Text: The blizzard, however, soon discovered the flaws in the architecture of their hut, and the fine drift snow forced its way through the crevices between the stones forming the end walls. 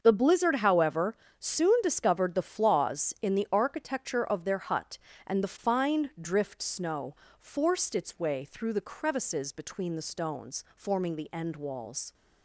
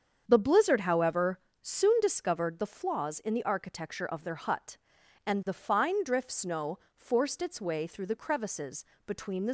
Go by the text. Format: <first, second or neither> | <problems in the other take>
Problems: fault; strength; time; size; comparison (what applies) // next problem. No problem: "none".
first | starts louder than the rest; strong; until 1.2 s; 7.5 dB; also in the first // pauses between "snow" and "forced"; slight; at 6.7 s; 0.18 s long; slight in the first // pauses between "crevices" and "between"; slight; at 8.8 s; 0.22 s long // stops before "stones forming the end walls"; at 9.4 s